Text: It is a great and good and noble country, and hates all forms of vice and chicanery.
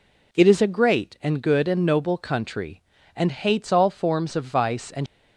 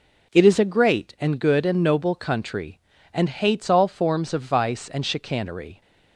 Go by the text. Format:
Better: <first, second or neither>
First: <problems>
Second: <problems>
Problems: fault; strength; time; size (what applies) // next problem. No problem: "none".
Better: second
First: stops before "chicanery"; at 5.0 s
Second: none